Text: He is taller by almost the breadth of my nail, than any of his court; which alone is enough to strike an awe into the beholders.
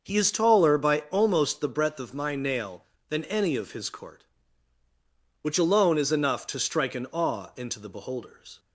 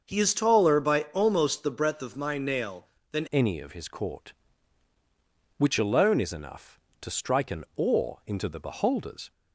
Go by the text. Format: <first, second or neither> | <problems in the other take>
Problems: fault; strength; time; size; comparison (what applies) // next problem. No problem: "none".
first | starts louder than the rest; until 1.1 s; 6.5 dB; noticeable in the first // changes voice at "any"; from 3.3 s on; 6.0 s long